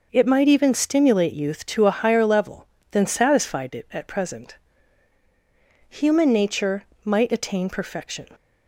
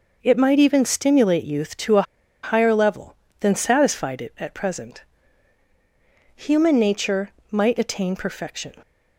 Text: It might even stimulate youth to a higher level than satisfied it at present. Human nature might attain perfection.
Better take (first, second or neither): first